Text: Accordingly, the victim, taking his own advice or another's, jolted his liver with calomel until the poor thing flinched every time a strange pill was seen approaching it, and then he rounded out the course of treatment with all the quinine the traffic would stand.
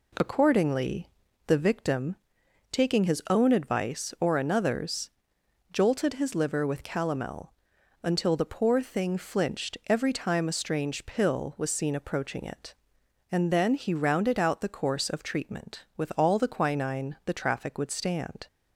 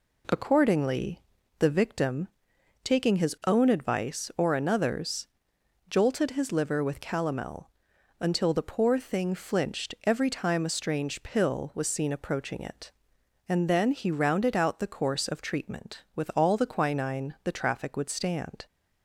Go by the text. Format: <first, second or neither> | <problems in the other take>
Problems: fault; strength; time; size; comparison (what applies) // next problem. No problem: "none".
neither | pauses between "calomel" and "until"; noticeable; the same in both